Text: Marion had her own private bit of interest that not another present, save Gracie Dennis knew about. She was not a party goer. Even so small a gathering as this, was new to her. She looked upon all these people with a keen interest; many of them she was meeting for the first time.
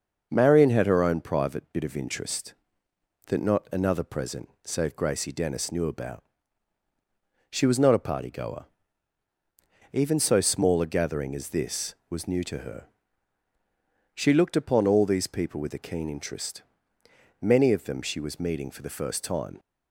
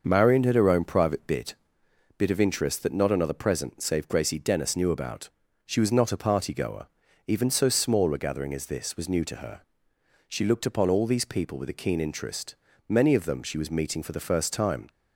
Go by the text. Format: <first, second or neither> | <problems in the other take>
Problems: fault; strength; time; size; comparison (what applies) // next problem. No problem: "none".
first | starts louder than the rest; until 1.0 s; 6 dB; also in the first // says "bit" twice; at 2.1 s